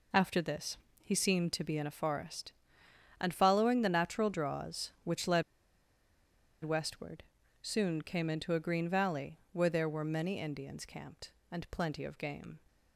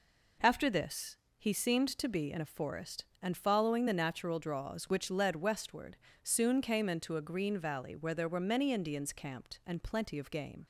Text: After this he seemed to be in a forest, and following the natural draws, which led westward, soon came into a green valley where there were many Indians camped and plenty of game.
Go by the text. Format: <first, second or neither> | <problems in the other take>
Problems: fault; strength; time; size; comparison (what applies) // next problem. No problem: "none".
second | pauses between "this" and "he"; slight; at 0.7 s; 0.26 s long; slight in the second // pauses between "led" and "westward"; at 5.4 s; 1.2 s long